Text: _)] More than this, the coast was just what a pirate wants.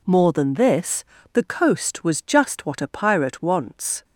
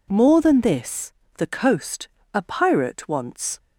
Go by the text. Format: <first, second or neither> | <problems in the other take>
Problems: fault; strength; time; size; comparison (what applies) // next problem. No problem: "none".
first | skips "was just what"; at 2.1 s